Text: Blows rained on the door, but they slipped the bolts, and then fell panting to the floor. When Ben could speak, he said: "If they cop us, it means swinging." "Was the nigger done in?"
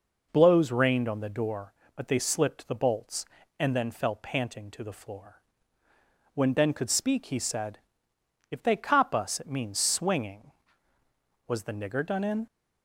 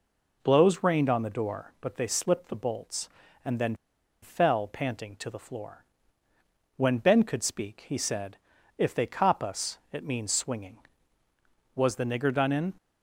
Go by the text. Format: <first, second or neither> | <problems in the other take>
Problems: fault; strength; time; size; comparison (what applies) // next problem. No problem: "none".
first | pauses between "then" and "fell"; noticeable; at 3.7 s; 0.48 s long